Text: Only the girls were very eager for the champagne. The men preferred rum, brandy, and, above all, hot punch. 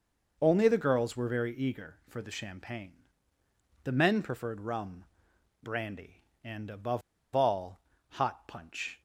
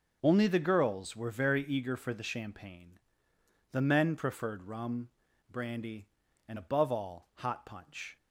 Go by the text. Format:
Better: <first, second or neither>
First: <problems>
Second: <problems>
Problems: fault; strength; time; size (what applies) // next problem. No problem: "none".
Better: second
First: pauses between "above" and "all"; slight; at 7.0 s; 0.33 s long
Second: none